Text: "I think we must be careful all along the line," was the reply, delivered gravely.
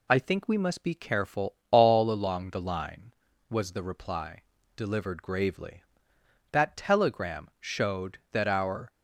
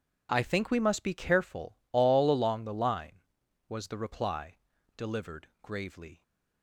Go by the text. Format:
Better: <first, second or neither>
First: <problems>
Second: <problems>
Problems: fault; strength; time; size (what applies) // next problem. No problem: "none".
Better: second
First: goes on to say "That telegram showed that our"; strong; from 6.5 s on; 2.4 s long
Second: none